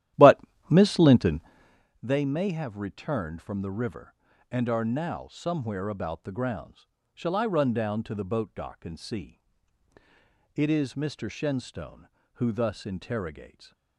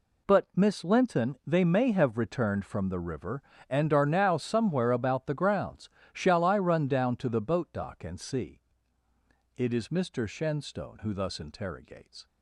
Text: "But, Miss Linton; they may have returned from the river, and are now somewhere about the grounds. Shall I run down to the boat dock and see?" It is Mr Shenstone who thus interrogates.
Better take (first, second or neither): second